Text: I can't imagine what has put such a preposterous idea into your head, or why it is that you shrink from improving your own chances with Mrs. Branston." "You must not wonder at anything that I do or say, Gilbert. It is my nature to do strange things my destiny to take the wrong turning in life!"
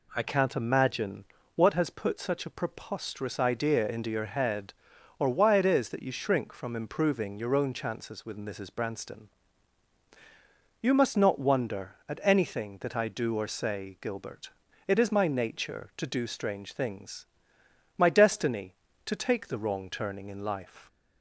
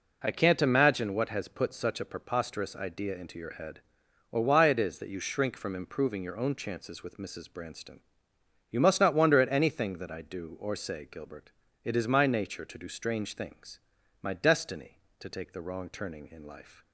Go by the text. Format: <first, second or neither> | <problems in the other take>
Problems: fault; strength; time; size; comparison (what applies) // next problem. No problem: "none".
second | changes voice at "can't"; from 0.2 s on; 20.6 s long // pauses between "imagine" and "what"; slight; at 1.2 s; 0.30 s long // pauses between "things" and "my"; noticeable; at 17.2 s; 0.72 s long; also in the second